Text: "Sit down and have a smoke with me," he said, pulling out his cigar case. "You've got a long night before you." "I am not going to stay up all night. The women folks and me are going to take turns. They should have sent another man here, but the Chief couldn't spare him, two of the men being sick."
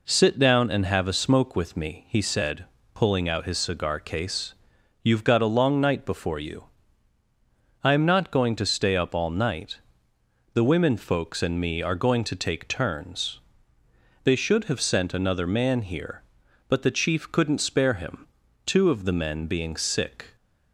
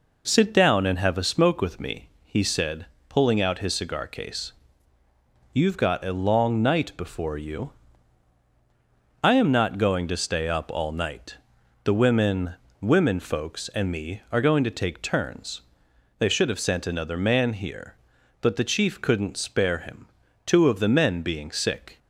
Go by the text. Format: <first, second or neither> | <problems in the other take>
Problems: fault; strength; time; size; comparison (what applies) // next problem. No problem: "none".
first | says "women" twice; at 12.8 s